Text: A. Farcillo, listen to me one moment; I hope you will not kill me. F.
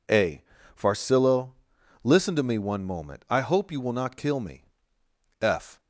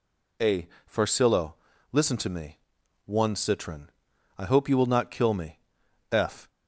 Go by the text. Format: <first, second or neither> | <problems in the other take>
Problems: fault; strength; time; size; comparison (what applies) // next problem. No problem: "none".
first | pauses between "me" and "one"; noticeable; at 2.5 s; 0.48 s long // says "citron" for "moment"; at 3.3 s